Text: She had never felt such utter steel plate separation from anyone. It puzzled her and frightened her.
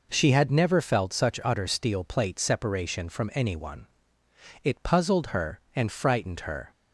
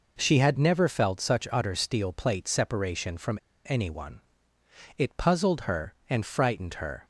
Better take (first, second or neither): first